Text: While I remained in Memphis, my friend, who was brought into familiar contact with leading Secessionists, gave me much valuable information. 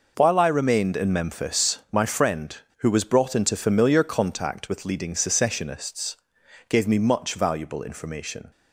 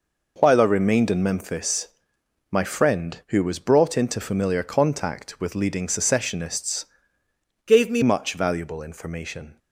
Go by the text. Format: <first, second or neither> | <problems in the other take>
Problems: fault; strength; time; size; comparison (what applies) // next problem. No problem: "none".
first | changes voice from "gave" to "me"; from 7.6 to 8.0 s; 0.4 s long